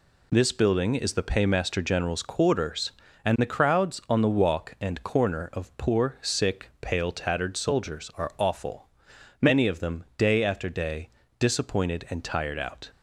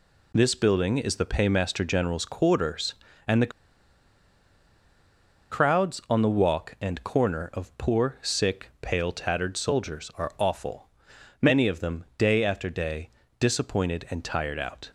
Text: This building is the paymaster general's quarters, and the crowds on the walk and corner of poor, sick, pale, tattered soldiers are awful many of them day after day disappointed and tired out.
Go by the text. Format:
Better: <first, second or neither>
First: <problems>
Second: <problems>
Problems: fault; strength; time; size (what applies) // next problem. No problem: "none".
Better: first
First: pauses between "awful" and "many"; noticeable; at 8.8 s; 0.54 s long // pauses between "day" and "disappointed"; slight; at 11.0 s; 0.30 s long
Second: pauses between "the" and "crowds"; strong; at 3.5 s; 2.0 s long // pauses between "awful" and "many"; noticeable; at 10.8 s; 0.54 s long // pauses between "day" and "disappointed"; slight; at 13.0 s; 0.30 s long